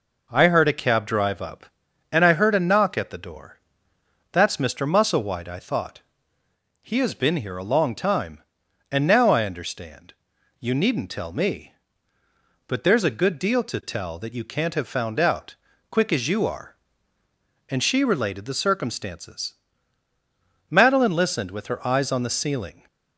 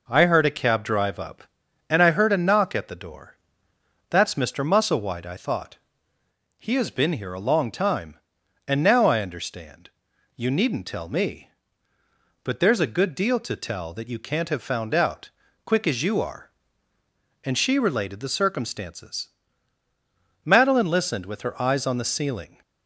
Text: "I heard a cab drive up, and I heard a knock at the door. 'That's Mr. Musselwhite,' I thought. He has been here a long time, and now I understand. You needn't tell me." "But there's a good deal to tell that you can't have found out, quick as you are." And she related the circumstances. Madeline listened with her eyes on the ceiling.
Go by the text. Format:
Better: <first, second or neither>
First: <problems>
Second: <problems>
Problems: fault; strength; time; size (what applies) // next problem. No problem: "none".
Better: neither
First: none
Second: none